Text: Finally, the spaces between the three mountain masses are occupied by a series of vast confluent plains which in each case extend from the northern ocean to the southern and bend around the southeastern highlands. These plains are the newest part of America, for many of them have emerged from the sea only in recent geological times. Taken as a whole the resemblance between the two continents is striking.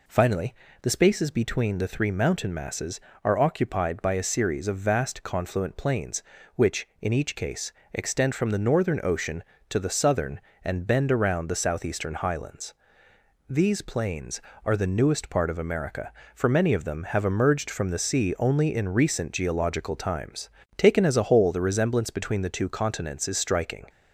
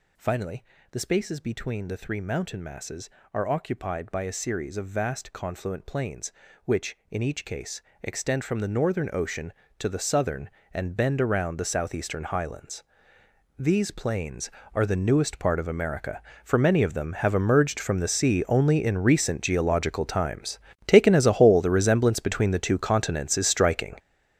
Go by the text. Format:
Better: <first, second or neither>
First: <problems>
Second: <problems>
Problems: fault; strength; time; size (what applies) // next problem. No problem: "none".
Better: first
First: pauses between "case" and "extend"; slight; at 7.7 s; 0.20 s long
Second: gets louder; strong; throughout; 12 dB // pauses between "case" and "extend"; slight; at 7.8 s; 0.20 s long